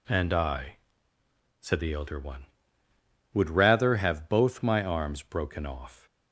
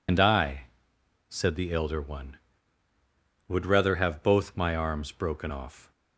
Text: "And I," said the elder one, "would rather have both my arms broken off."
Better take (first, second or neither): first